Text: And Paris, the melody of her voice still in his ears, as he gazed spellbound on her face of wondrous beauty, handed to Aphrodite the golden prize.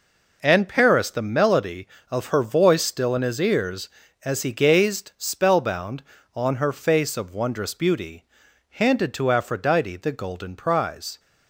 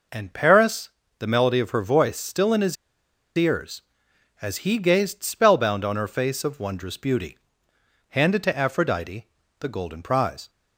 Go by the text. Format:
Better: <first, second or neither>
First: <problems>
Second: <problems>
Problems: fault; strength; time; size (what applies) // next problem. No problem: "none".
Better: first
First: none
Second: pauses between "his" and "ears"; noticeable; at 2.7 s; 0.61 s long // pauses between "Aphrodite" and "the"; slight; at 9.2 s; 0.32 s long